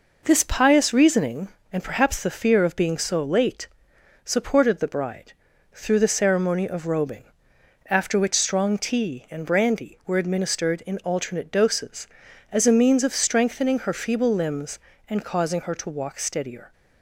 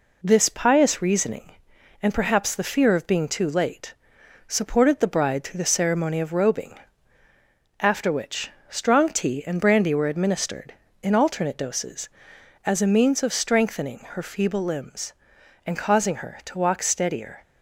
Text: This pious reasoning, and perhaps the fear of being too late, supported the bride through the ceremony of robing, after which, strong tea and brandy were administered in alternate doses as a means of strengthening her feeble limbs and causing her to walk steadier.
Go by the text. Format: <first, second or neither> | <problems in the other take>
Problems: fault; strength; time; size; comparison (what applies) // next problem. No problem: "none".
second | says "so" for "too"; at 2.9 s // pauses between "bride" and "through"; at 5.3 s; 0.40 s long